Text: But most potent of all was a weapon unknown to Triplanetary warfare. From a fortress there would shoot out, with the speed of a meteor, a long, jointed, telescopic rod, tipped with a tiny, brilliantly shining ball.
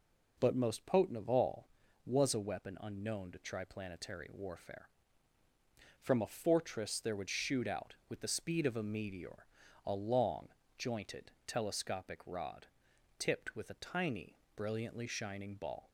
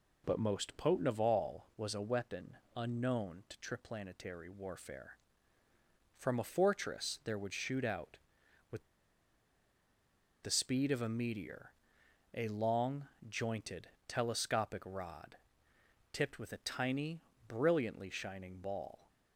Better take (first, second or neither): first